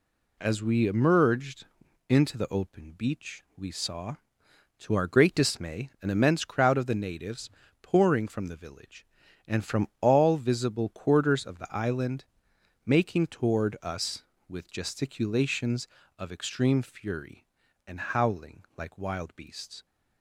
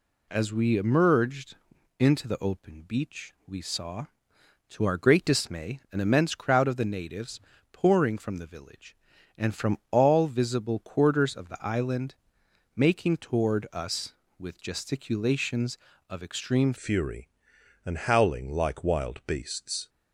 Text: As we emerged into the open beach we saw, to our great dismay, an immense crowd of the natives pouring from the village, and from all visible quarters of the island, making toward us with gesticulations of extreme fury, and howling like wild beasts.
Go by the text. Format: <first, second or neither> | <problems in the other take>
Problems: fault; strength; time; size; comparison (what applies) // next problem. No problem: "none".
first | pauses between "emerged" and "into"; noticeable; at 1.5 s; 0.46 s long; noticeable in the first // pauses between "natives" and "pouring"; slight; at 7.3 s; 0.32 s long; slight in the first // changes voice at "fury"; from 16.7 s on; 3.1 s long